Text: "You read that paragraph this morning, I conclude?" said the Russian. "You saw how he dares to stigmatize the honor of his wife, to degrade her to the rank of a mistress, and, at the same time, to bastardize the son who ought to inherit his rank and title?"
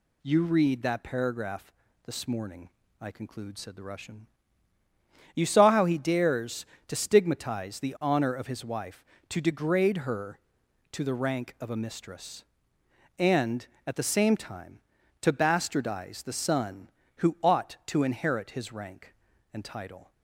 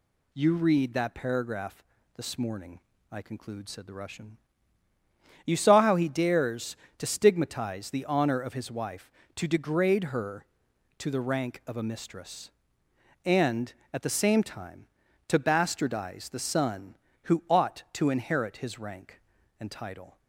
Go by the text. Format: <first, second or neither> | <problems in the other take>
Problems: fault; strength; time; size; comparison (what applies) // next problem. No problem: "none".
neither | pauses between "paragraph" and "this"; slight; the same in both